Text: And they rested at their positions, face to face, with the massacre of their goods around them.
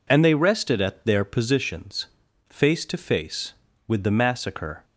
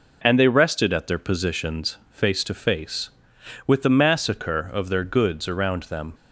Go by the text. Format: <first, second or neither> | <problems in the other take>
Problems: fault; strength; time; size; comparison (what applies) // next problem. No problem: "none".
second | stops before "of their goods around them"; at 4.8 s